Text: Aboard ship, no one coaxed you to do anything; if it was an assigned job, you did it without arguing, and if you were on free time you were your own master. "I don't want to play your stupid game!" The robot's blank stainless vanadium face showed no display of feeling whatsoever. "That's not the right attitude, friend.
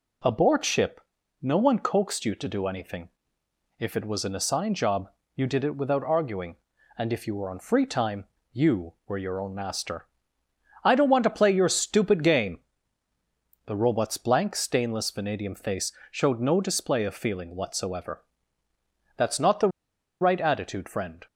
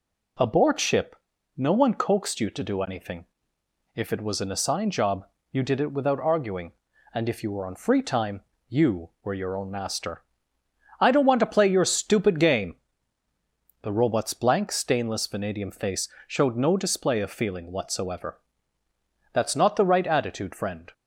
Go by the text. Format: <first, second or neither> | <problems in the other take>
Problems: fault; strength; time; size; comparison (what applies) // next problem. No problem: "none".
second | pauses between "time" and "you"; slight; at 8.2 s; 0.28 s long; slight in the second // pauses between "face" and "showed"; slight; at 15.9 s; 0.18 s long; slight in the second // pauses between "the" and "right"; noticeable; at 19.6 s; 0.52 s long